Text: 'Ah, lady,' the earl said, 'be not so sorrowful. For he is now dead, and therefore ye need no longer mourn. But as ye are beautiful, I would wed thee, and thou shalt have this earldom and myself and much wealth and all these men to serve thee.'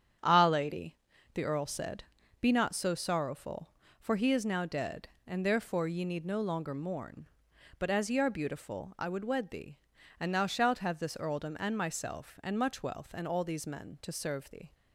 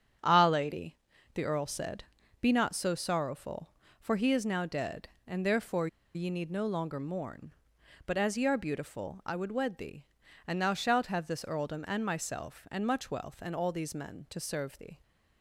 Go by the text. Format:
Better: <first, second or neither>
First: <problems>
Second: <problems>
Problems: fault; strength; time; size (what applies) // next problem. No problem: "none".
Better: first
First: starts louder than the rest; strong; until 1.5 s; 8.5 dB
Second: starts louder than the rest; strong; until 1.5 s; 8 dB // pauses between "therefore" and "ye"; slight; at 5.8 s; 0.28 s long